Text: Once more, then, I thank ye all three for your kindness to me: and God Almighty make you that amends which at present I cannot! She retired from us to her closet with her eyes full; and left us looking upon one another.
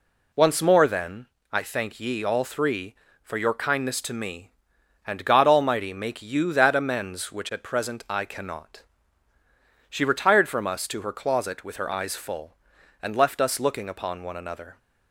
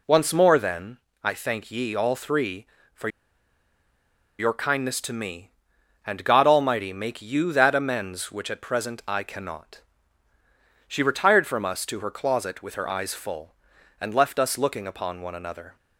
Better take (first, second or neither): first